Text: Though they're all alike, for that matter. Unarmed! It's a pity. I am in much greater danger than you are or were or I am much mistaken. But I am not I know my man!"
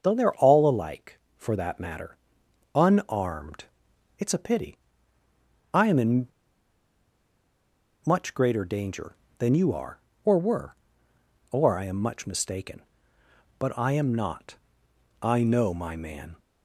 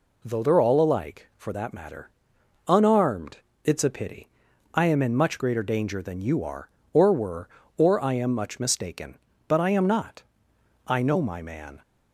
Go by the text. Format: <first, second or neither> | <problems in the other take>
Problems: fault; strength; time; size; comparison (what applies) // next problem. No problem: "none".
second | starts louder than the rest; until 1.0 s; 6.5 dB // pauses between "in" and "much"; strong; at 6.2 s; 1.7 s long // pauses between "not" and "I"; noticeable; at 14.5 s; 0.66 s long; noticeable in the second